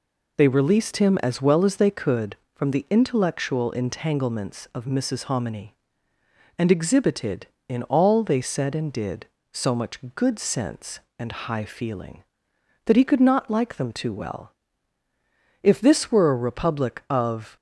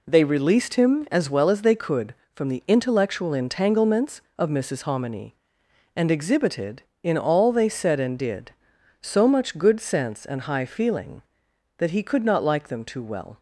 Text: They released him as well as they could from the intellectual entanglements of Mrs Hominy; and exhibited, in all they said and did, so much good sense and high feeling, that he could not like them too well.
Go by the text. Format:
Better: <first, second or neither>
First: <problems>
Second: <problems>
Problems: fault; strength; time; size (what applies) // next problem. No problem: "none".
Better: second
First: pauses between "much" and "good"; slight; at 9.9 s; 0.16 s long // goes on to say "If this were a republic of"; strong; from 15.6 s on; 1.9 s long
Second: none